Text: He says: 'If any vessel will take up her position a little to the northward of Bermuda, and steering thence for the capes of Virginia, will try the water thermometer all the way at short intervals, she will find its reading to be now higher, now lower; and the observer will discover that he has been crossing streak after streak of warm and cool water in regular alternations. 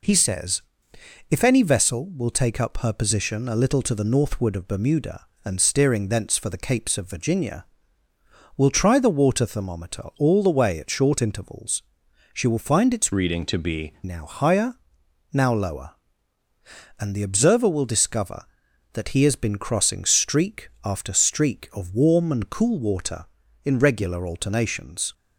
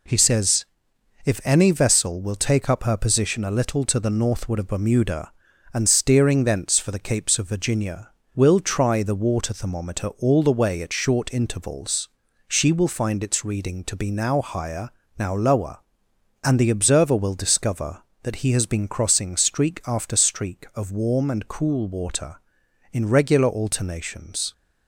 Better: second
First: changes voice from "reading" to "be"; from 13.1 to 13.9 s; 0.8 s long // pauses between "streak" and "after"; slight; at 20.6 s; 0.16 s long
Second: none

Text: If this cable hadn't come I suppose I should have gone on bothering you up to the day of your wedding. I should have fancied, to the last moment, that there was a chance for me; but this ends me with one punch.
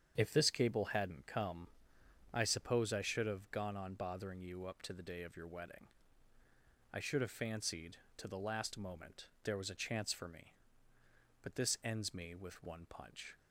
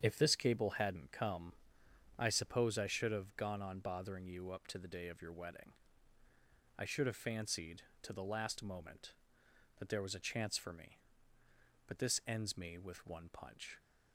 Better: second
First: starts louder than the rest; strong; until 1.1 s; 8 dB // pauses between "come" and "I"; noticeable; at 1.6 s; 0.64 s long // skips "that"; at 9.3 s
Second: starts louder than the rest; strong; until 1.0 s; 8 dB // pauses between "come" and "I"; noticeable; at 1.5 s; 0.64 s long

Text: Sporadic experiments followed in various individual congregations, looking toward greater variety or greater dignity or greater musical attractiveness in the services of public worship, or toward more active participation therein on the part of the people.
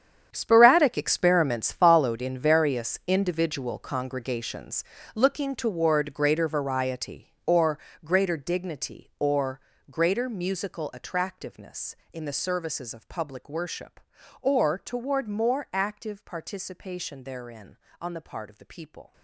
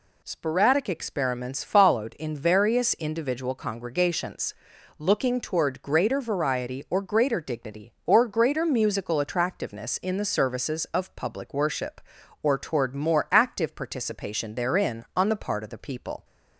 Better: second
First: gets quieter; strong; throughout; 14 dB // pauses between "or" and "greater"; slight; at 7.8 s; 0.24 s long // pauses between "or" and "greater"; slight; at 9.5 s; 0.32 s long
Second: none

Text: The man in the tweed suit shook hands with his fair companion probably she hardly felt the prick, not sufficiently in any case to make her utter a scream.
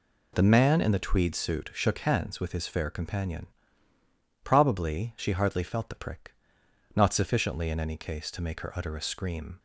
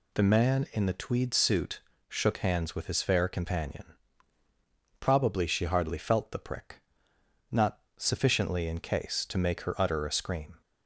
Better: first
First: pauses between "companion" and "probably"; noticeable; at 3.4 s; 0.98 s long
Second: pauses between "suit" and "shook"; slight; at 1.8 s; 0.30 s long // pauses between "companion" and "probably"; at 3.8 s; 1.1 s long // pauses between "not" and "sufficiently"; slight; at 7.8 s; 0.16 s long // skips "any"; at 8.7 s

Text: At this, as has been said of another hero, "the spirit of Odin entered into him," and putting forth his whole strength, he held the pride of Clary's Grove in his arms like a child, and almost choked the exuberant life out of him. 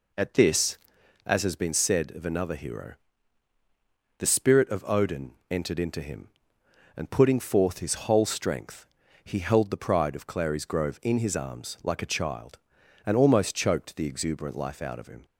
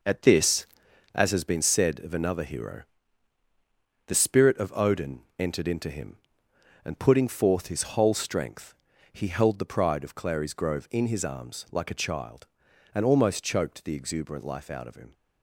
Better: first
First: pauses between "Odin" and "entered"; slight; at 5.3 s; 0.16 s long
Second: gets quieter; strong; throughout; 7.5 dB // pauses between "Odin" and "entered"; slight; at 5.2 s; 0.16 s long

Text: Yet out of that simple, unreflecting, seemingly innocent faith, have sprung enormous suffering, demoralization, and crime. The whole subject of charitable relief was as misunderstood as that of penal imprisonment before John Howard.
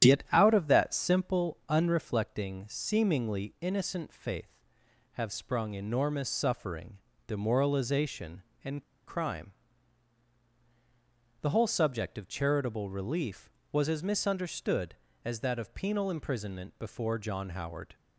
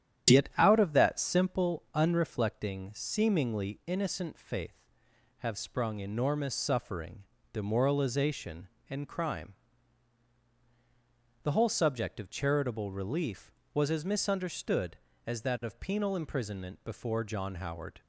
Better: second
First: starts louder than the rest; strong; until 1.1 s; 9.5 dB // pauses between "and" and "crime"; slight; at 8.8 s; 0.24 s long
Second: starts louder than the rest; strong; until 1.3 s; 9.5 dB

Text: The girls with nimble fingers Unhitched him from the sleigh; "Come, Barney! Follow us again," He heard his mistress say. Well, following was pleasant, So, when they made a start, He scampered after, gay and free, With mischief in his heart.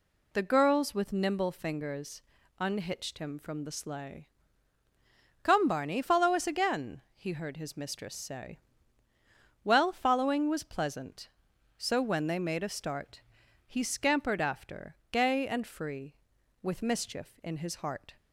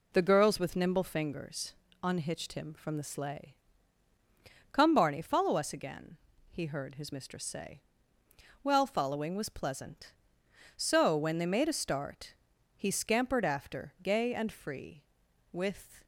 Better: first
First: pauses between "fingers" and "Unhitched"; at 2.2 s; 0.38 s long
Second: pauses between "fingers" and "Unhitched"; slight; at 1.7 s; 0.28 s long // stops before "mischief in his heart"; at 16.0 s

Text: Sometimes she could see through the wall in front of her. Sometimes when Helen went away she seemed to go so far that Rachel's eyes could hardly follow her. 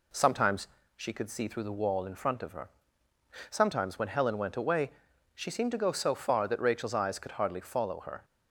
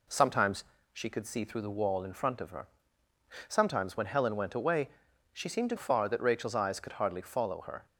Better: first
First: pauses between "Sometimes" and "she"; slight; at 0.6 s; 0.28 s long // pauses between "away" and "she"; noticeable; at 4.9 s; 0.46 s long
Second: pauses between "Sometimes" and "she"; slight; at 0.6 s; 0.28 s long // pauses between "away" and "she"; noticeable; at 4.8 s; 0.46 s long // skips "go so"; at 5.7 s

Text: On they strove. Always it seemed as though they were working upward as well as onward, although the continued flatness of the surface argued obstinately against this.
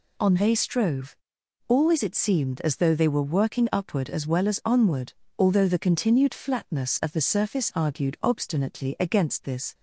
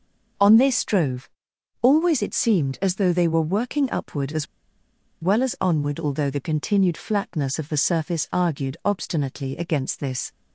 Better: first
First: none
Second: pauses between "as" and "well"; noticeable; at 4.4 s; 0.78 s long

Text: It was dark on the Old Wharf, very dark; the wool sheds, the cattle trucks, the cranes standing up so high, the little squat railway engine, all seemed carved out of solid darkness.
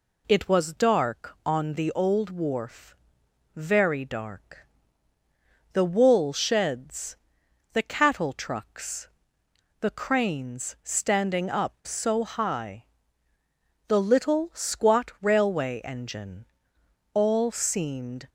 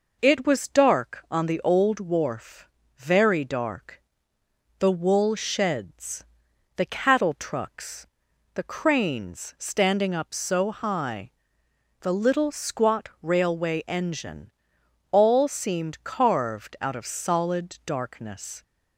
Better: second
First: stops before "carved out of solid darkness"; at 18.2 s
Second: none

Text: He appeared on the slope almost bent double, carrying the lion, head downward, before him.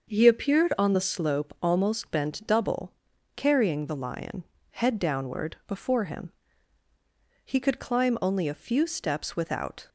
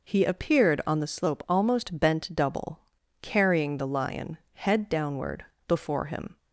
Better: second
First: starts louder than the rest; until 1.1 s; 6.5 dB // goes on to say "He could climb only a few steps without"; strong; from 7.4 s on; 2.4 s long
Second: none

